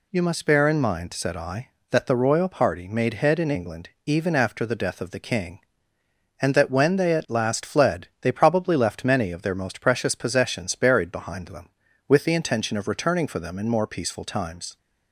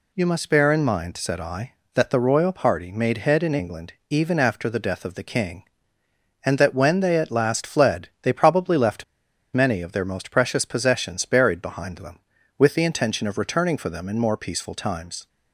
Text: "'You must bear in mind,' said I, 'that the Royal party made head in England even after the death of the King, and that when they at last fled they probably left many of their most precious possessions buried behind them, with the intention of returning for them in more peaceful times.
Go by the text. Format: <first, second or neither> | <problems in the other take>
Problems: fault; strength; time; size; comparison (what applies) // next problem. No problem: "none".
first | pauses between "England" and "even"; slight; at 3.9 s; 0.16 s long; slight in the first // pauses between "left" and "many"; noticeable; at 9.0 s; 0.50 s long